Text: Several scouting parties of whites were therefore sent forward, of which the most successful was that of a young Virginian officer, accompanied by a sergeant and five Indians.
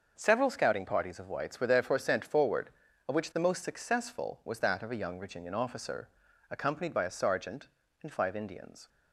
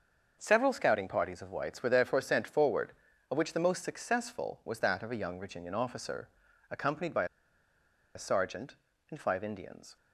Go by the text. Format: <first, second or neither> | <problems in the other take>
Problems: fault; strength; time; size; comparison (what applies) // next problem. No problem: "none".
first | starts louder than the rest; until 1.4 s; 6.5 dB; also in the first // pauses between "by" and "a"; noticeable; at 7.2 s; 0.90 s long